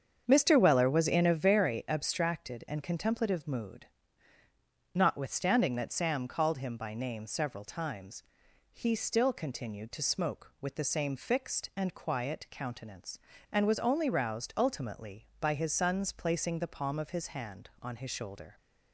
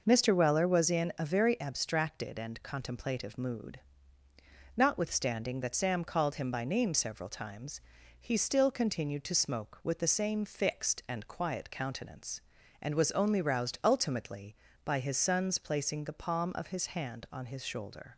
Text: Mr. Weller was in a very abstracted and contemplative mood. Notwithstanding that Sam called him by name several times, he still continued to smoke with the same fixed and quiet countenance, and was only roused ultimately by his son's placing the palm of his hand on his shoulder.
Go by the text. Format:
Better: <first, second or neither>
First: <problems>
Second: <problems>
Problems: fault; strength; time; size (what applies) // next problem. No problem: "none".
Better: second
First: starts louder than the rest; strong; until 1.4 s; 7.5 dB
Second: none